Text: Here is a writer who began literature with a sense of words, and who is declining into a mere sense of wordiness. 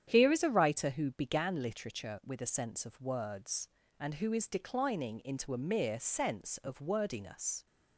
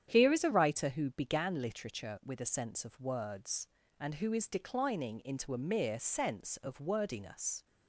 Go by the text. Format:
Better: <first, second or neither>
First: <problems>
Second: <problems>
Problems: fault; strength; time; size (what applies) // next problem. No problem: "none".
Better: neither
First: starts louder than the rest; strong; until 1.0 s; 9 dB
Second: starts louder than the rest; strong; until 1.1 s; 9 dB